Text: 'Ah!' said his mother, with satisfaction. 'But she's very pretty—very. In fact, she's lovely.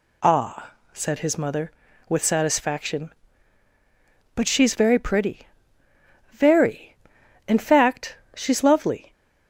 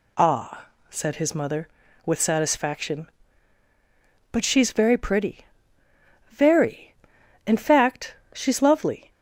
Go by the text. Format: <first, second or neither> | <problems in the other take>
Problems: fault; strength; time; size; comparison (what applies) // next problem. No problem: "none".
neither | none